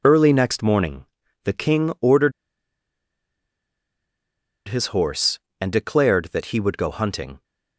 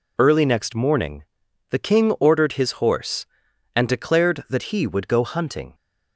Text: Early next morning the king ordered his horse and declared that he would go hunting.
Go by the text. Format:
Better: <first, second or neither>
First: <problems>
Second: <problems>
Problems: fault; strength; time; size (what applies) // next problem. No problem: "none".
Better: second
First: pauses between "morning" and "the"; at 1.0 s; 0.38 s long // pauses between "ordered" and "his"; strong; at 2.3 s; 2.3 s long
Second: pauses between "morning" and "the"; noticeable; at 1.2 s; 0.46 s long